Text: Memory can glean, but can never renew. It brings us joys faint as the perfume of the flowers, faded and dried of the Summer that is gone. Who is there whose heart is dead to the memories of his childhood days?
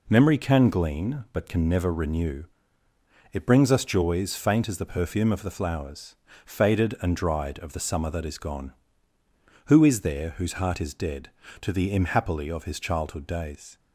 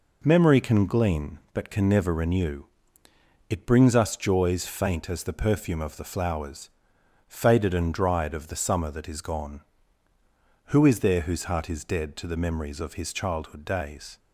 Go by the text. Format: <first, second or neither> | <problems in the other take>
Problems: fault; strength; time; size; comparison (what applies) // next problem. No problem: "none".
second | says "imhappily" for "memories"; at 11.9 s